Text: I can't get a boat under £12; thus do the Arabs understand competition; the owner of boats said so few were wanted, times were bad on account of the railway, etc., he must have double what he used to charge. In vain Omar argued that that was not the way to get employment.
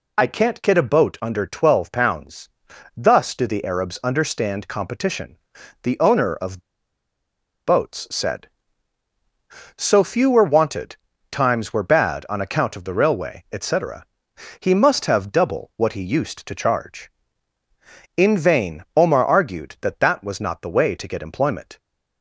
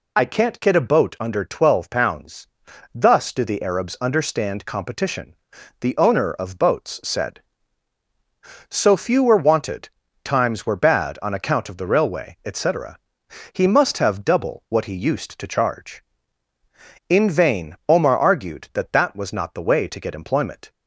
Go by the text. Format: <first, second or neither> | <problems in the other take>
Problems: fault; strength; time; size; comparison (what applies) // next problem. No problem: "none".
second | pauses between "of" and "boats"; at 6.5 s; 1.0 s long